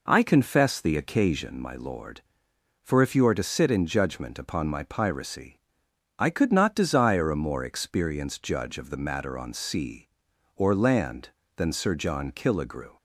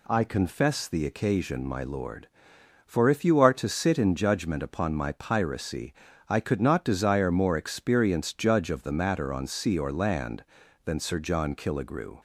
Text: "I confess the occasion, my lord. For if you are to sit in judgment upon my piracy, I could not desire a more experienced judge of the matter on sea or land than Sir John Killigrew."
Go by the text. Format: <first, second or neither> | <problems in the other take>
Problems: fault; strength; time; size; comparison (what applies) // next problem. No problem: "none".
first | skips "a"; at 7.3 s